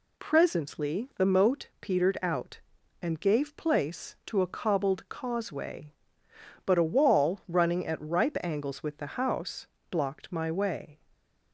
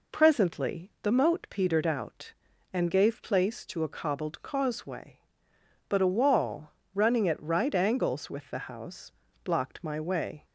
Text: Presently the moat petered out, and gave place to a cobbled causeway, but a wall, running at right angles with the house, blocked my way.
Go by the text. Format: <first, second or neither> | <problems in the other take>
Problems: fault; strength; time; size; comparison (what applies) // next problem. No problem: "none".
second | says "ripe" for "right"; at 8.0 s